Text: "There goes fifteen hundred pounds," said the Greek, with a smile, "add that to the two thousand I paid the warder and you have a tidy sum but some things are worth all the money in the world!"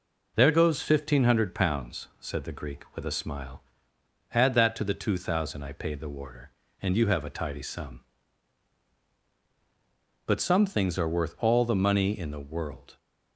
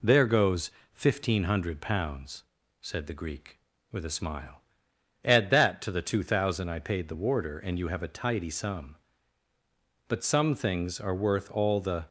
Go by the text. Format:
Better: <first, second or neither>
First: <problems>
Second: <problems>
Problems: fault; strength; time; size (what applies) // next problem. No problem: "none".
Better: first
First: none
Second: pauses between "goes" and "fifteen"; slight; at 0.7 s; 0.24 s long // stops before "money in the world"; at 12.0 s